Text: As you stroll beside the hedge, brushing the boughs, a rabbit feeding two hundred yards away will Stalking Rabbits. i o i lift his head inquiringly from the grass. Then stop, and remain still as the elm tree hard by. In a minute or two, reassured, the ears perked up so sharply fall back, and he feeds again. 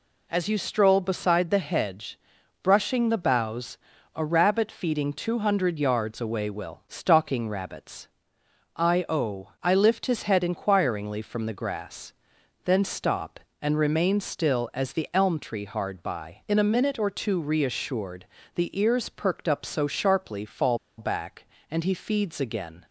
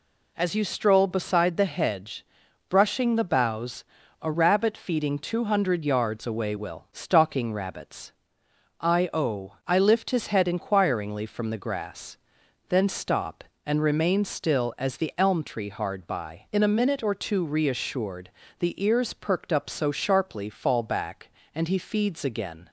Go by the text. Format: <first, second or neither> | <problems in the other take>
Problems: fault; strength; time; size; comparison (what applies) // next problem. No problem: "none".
second | pauses between "fall" and "back"; slight; at 20.7 s; 0.20 s long